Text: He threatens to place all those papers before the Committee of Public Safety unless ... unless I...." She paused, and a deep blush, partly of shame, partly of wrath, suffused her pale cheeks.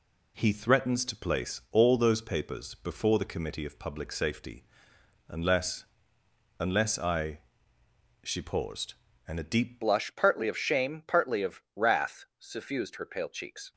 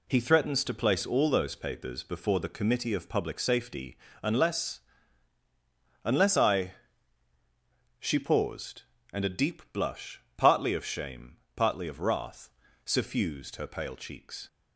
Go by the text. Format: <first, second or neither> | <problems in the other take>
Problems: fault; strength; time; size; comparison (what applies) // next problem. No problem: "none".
second | pauses between "Safety" and "unless"; noticeable; at 4.6 s; 0.64 s long; slight in the second // changes voice at "blush"; from 9.8 s on; 3.9 s long